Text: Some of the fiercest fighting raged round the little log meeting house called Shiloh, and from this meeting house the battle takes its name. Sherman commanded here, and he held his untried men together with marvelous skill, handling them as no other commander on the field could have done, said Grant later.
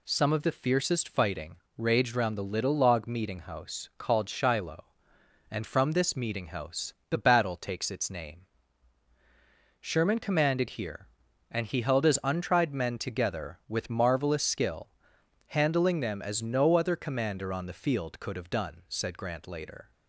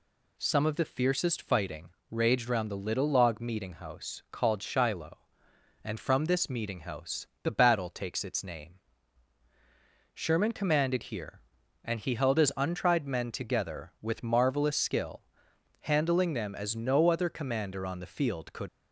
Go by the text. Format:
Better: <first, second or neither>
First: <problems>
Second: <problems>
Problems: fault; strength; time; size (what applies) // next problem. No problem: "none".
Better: first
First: pauses between "fighting" and "raged"; slight; at 1.5 s; 0.20 s long // pauses between "house" and "the"; slight; at 6.9 s; 0.18 s long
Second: pauses between "fighting" and "raged"; slight; at 1.9 s; 0.20 s long // pauses between "house" and "the"; slight; at 7.2 s; 0.18 s long // stops before "have done said Grant later"; at 18.6 s